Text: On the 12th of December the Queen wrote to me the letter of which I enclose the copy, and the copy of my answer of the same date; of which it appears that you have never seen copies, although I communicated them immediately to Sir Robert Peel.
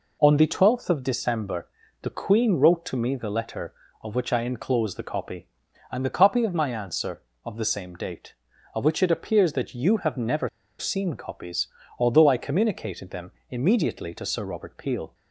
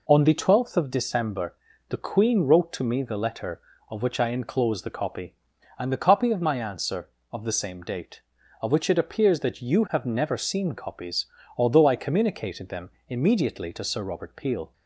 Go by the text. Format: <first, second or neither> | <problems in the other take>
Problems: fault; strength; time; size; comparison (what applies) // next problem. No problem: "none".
second | pauses between "December" and "the"; slight; at 1.6 s; 0.36 s long; slight in the second // pauses between "never" and "seen"; slight; at 10.4 s; 0.30 s long // pauses between "them" and "immediately"; slight; at 13.3 s; 0.16 s long; slight in the second